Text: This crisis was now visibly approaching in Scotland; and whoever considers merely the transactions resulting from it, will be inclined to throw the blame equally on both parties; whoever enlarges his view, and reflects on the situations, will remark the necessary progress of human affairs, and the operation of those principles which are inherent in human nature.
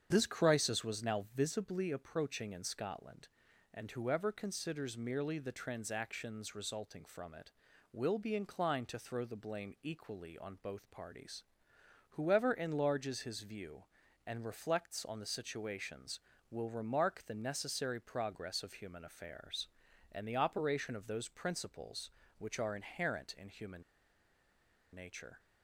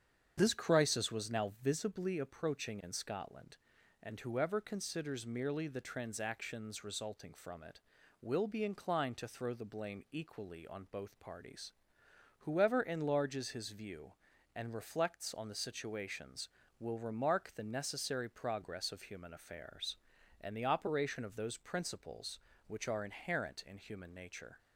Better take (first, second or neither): second